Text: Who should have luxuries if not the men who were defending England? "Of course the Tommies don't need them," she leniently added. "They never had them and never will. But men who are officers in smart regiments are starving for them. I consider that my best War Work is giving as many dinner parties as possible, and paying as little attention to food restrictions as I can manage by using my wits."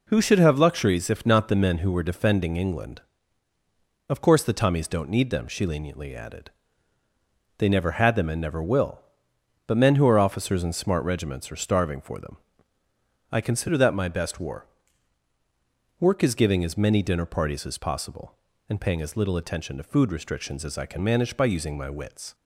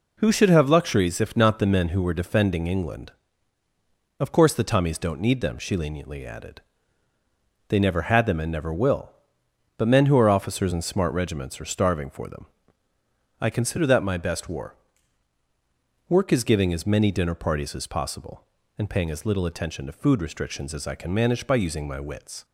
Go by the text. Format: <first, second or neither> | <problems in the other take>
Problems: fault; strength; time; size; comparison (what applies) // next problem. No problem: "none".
neither | pauses between "War" and "Work"; strong; the same in both